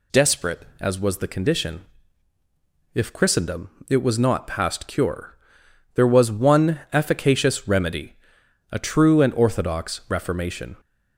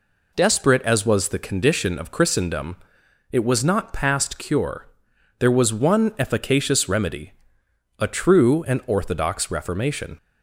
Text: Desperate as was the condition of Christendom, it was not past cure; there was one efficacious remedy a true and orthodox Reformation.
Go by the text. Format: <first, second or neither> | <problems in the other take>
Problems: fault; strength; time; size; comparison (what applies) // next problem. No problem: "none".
second | says "if" for "of"; at 2.9 s // pauses between "remedy" and "a"; noticeable; at 8.1 s; 0.58 s long; noticeable in the second